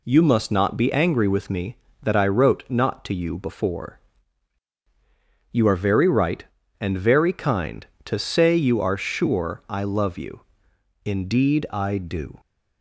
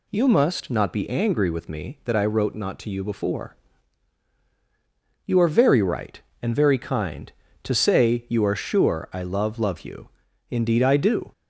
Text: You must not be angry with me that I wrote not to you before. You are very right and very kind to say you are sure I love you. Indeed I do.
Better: first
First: none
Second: says "love" twice; at 9.5 s

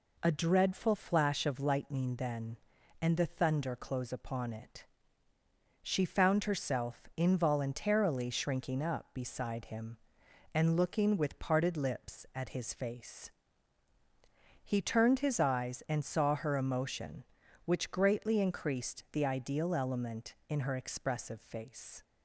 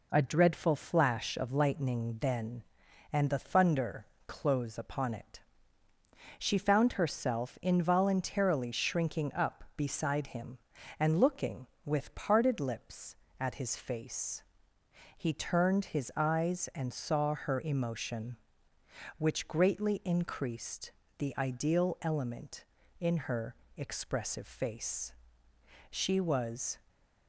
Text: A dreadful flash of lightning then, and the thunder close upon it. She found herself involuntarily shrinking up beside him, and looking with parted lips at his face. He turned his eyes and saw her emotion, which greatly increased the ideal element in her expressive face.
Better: first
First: none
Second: pauses between "thunder" and "close"; slight; at 4.0 s; 0.20 s long // pauses between "increased" and "the"; slight; at 20.9 s; 0.28 s long // goes on to say "She was"; noticeable; from 25.9 s on; 0.88 s long

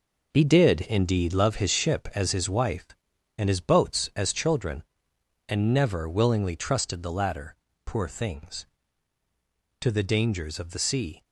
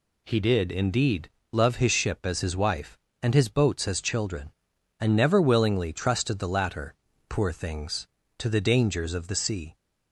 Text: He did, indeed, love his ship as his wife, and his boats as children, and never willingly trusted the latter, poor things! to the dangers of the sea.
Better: second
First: gets quieter; strong; throughout; 9 dB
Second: none

